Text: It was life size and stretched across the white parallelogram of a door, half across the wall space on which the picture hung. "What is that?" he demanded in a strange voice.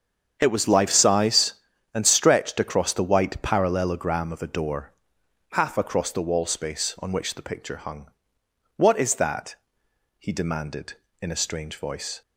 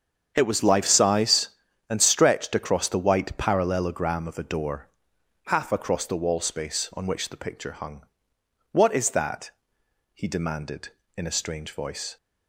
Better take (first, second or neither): neither